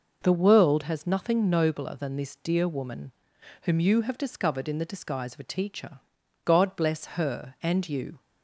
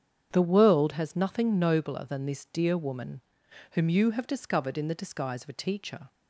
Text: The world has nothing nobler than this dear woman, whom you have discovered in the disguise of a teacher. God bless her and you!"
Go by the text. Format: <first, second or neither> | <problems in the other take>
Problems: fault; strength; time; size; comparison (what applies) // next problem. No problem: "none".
first | starts louder than the rest; strong; until 1.3 s; 8 dB // stops before "God bless her and you"; at 6.0 s